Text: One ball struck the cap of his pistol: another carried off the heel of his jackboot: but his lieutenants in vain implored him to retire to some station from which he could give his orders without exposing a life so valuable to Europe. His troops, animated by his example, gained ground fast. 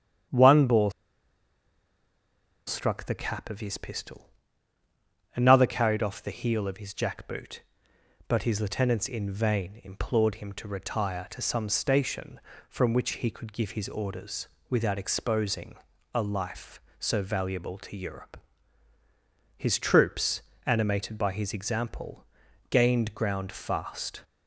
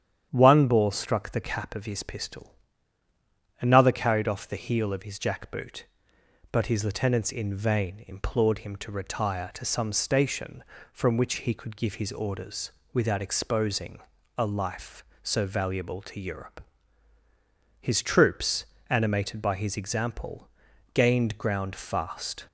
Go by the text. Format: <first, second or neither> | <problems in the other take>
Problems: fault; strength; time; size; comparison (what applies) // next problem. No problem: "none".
second | starts louder than the rest; strong; until 3.0 s; 9.5 dB; strong in the second // pauses between "ball" and "struck"; strong; at 0.9 s; 1.7 s long // pauses between "orders" and "without"; slight; at 14.4 s; 0.20 s long; slight in the second // pauses between "exposing" and "a"; at 15.7 s; 0.38 s long; also in the second